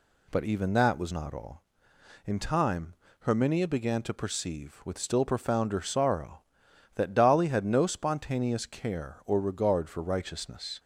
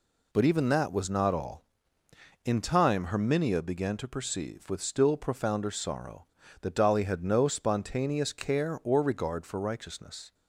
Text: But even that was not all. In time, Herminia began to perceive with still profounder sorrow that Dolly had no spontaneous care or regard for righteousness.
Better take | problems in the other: neither | none

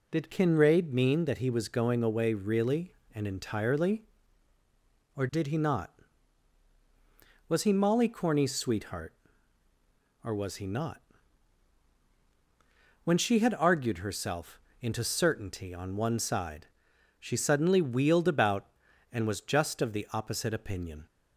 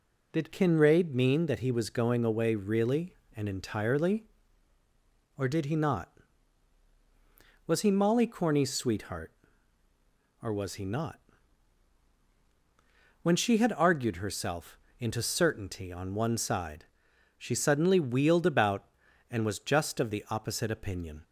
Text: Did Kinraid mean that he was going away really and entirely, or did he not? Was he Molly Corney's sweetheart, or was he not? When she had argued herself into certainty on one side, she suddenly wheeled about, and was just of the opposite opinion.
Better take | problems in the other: neither | pauses between "herself" and "into"; slight; the same in both

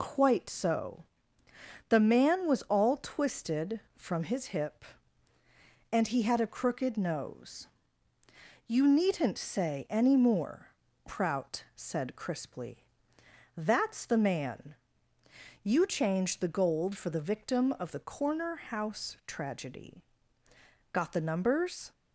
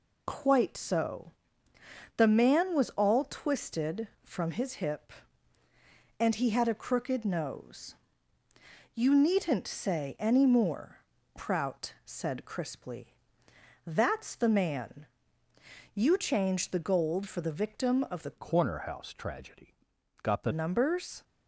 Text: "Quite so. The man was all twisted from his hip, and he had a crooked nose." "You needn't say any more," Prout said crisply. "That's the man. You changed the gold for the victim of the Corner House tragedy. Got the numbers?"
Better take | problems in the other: first | changes voice from "Corner" to "the"; from 18.3 to 20.5 s; 2.2 s long

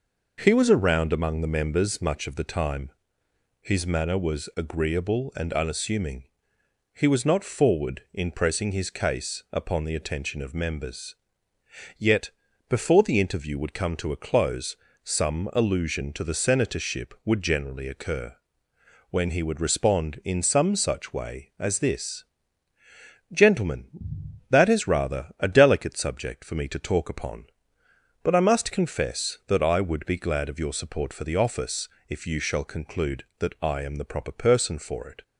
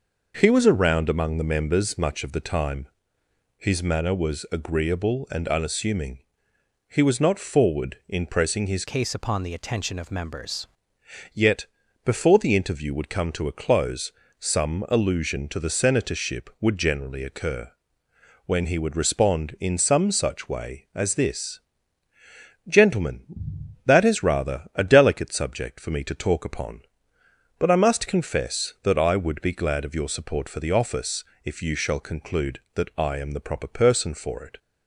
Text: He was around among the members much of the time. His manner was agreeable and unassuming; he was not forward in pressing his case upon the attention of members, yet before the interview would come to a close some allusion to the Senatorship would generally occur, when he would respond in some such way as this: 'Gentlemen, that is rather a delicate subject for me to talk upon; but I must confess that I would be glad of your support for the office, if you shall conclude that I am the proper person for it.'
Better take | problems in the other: first | changes voice from "case" to "members"; from 8.8 to 10.6 s; 1.8 s long // pauses between "yet" and "before"; at 11.6 s; 0.40 s long; also in the first // pauses between "close" and "some"; slight; at 14.1 s; 0.28 s long; slight in the first

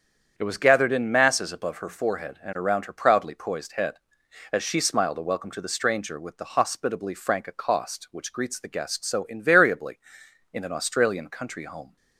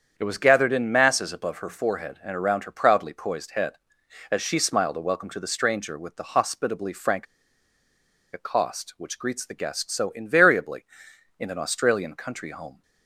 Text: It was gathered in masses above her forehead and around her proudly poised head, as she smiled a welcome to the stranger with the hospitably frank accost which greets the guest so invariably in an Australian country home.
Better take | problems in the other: first | starts louder than the rest; strong; until 1.1 s; 8 dB; strong in the first // pauses between "frank" and "accost"; at 7.2 s; 1.0 s long

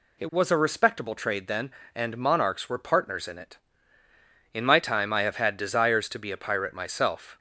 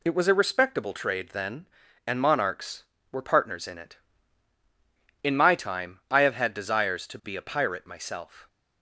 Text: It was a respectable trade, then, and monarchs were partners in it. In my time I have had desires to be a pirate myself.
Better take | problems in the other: neither | none

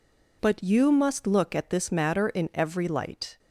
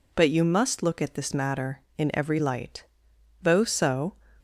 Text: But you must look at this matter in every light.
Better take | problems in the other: first | goes on to say "Though so"; noticeable; from 3.4 s on; 0.72 s long

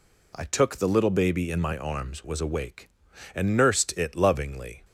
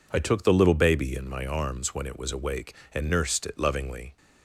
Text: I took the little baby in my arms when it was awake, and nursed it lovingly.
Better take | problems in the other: second | skips "when it"; at 2.2 s

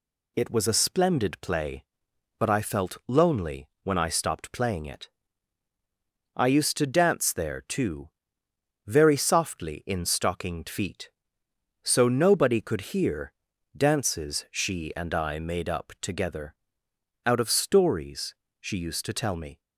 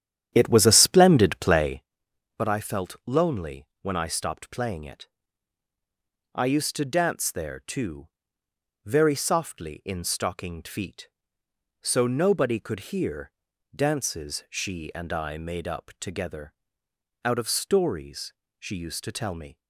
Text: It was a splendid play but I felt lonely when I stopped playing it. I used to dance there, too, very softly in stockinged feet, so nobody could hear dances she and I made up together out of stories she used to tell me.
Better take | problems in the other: first | starts louder than the rest; strong; until 1.9 s; 10.5 dB // pauses between "lonely" and "when"; slight; at 3.6 s; 0.16 s long; slight in the first // pauses between "hear" and "dances"; at 13.3 s; 0.42 s long; also in the first // pauses between "together" and "out"; noticeable; at 16.5 s; 0.70 s long; noticeable in the first // pauses between "stories" and "she"; slight; at 18.3 s; 0.26 s long; slight in the first

